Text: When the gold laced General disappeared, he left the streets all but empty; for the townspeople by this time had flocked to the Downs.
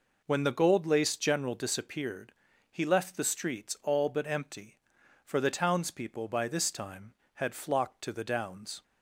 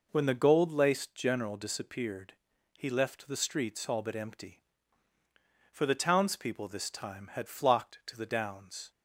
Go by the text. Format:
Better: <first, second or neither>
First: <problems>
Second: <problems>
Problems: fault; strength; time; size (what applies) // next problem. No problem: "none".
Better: first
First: none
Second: skips "by"; at 6.6 s